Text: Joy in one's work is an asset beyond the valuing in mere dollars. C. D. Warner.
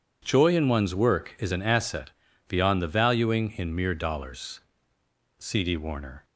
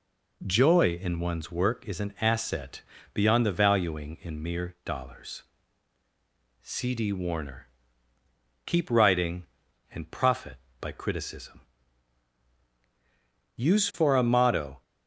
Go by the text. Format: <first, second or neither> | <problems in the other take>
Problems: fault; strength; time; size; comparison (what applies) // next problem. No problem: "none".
first | pauses between "asset" and "beyond"; slight; at 2.7 s; 0.34 s long; slight in the first // goes on to say "Keep writing and profit by criticism Use for a motto"; strong; from 8.6 s on; 6.1 s long